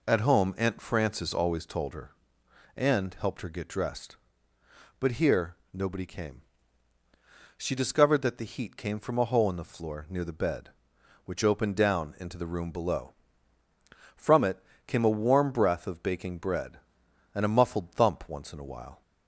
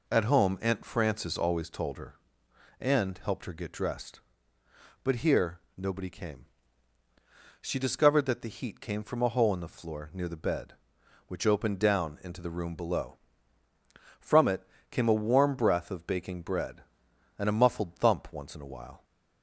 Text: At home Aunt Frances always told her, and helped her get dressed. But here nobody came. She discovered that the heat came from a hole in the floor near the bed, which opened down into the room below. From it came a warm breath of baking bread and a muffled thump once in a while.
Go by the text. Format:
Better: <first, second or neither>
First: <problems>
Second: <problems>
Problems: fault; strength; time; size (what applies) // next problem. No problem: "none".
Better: neither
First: pauses between "here" and "nobody"; slight; at 5.5 s; 0.18 s long // pauses between "it" and "came"; slight; at 14.5 s; 0.30 s long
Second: pauses between "here" and "nobody"; slight; at 5.5 s; 0.18 s long // pauses between "it" and "came"; slight; at 14.6 s; 0.30 s long